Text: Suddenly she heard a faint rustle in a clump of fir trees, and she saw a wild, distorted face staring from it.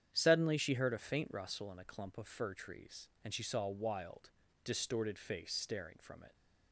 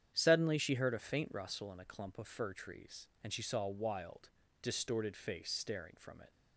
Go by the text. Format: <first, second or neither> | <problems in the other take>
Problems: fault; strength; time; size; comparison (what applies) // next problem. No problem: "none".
neither | starts louder than the rest; strong; the same in both